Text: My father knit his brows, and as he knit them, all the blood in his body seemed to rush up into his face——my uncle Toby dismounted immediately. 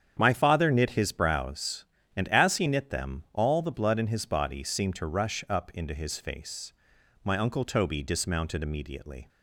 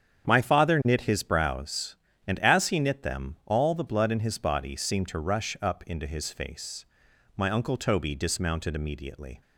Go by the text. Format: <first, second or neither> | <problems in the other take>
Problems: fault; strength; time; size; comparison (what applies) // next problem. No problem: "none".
neither | starts louder than the rest; strong; the same in both